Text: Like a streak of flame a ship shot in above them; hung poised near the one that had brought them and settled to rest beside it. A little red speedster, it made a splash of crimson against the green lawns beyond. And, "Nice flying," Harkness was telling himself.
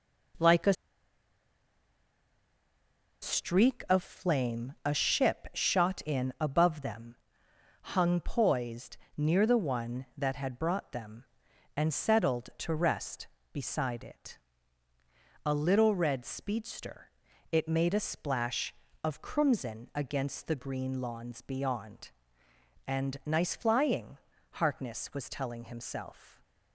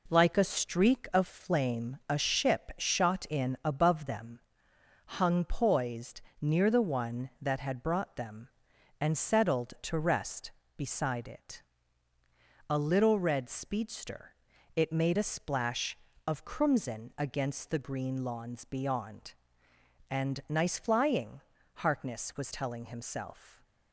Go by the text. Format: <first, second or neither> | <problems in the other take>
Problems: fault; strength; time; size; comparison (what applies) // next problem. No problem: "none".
second | pauses between "a" and "streak"; strong; at 0.7 s; 2.4 s long // pauses between "poised" and "near"; slight; at 8.9 s; 0.20 s long; slight in the second